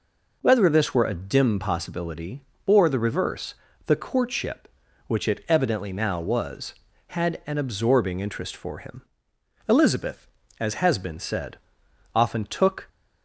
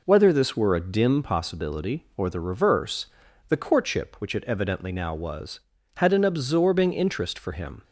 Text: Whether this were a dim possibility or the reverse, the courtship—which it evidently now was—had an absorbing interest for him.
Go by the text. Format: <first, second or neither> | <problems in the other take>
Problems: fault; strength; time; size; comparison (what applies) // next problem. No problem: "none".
second | goes on to say "Elizabeth as has been said often took"; strong; from 9.6 s on; 3.2 s long